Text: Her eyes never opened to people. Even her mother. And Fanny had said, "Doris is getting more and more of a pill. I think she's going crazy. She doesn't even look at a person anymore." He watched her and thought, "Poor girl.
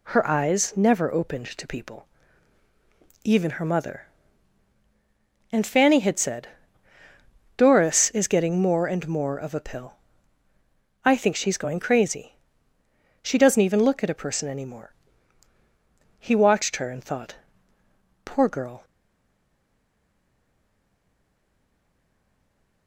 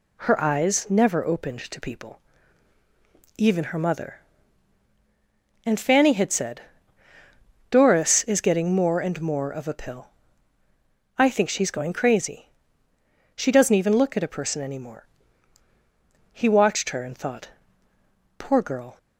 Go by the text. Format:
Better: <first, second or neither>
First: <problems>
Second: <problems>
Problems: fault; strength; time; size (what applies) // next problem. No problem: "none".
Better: second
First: stays silent after the last word; strong; from 18.8 s on; 4.0 s long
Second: none